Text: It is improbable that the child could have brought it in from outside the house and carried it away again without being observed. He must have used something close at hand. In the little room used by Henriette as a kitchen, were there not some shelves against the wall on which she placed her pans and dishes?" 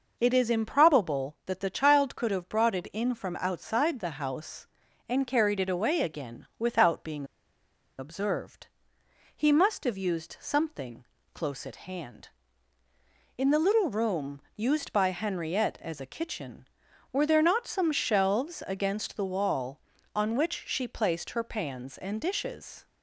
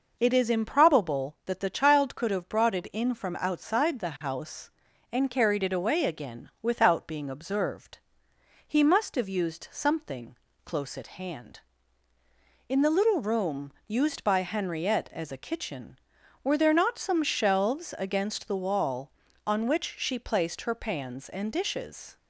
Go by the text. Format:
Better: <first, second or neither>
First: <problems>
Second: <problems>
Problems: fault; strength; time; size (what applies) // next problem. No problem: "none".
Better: second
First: pauses between "being" and "observed"; noticeable; at 7.2 s; 0.73 s long // pauses between "something" and "close"; slight; at 11.0 s; 0.26 s long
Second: pauses between "something" and "close"; slight; at 10.3 s; 0.26 s long